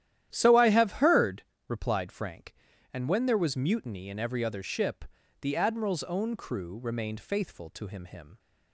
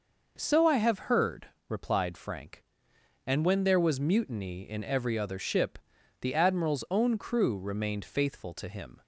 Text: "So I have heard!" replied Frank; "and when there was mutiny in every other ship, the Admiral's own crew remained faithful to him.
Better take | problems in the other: second | starts louder than the rest; strong; until 1.3 s; 11.5 dB // says "him" twice; at 8.0 s

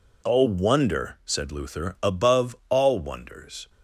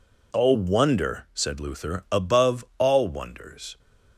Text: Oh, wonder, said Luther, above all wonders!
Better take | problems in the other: neither | none

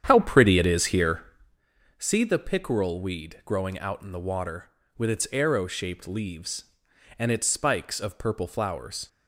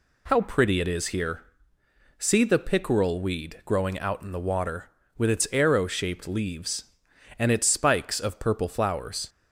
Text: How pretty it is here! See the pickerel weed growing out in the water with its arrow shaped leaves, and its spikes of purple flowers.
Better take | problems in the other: second | starts louder than the rest; strong; until 1.7 s; 9 dB

